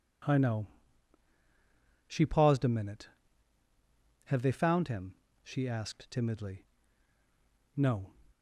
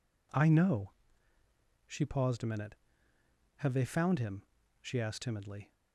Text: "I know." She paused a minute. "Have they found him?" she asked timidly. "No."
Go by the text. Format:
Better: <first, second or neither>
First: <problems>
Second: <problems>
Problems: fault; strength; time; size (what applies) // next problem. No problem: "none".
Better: first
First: none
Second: stops before "No"; at 5.7 s